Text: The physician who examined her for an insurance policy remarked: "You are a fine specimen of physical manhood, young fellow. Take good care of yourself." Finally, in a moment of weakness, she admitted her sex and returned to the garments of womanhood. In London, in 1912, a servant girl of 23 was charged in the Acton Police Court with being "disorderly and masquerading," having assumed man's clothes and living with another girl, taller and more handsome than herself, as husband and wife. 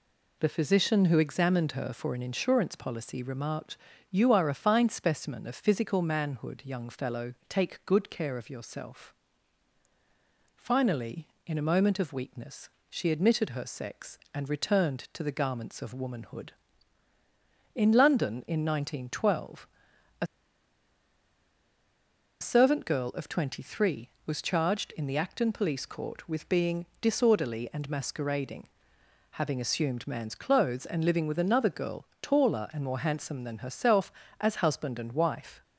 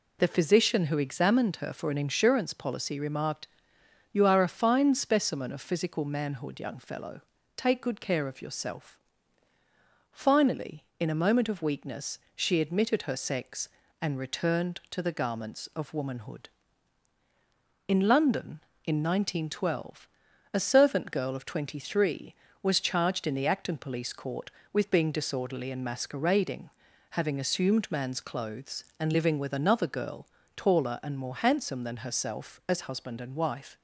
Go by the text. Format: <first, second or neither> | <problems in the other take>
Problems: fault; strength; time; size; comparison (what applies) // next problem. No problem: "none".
second | pauses between "a" and "servant"; strong; at 20.2 s; 2.1 s long